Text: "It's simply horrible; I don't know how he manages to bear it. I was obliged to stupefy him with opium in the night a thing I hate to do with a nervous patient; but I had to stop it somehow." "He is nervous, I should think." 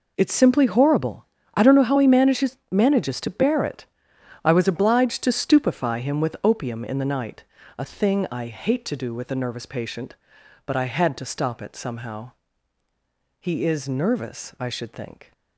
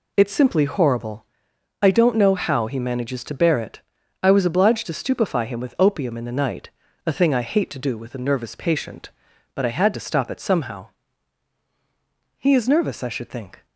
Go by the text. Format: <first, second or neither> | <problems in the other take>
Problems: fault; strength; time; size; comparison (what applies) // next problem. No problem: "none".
second | says "manages" twice; at 2.7 s // pauses between "night" and "a"; slight; at 7.4 s; 0.34 s long; also in the second